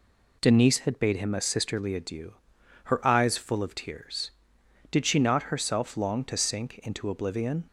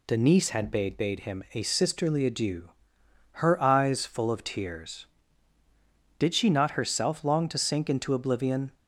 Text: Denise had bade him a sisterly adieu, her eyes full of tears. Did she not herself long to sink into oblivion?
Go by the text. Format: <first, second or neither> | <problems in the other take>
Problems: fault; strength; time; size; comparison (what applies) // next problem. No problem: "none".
first | says "bade" twice; at 0.9 s